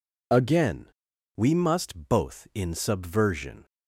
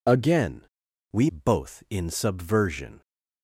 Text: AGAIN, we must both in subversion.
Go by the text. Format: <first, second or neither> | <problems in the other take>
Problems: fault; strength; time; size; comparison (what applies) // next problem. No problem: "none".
first | skips "must"; at 1.2 s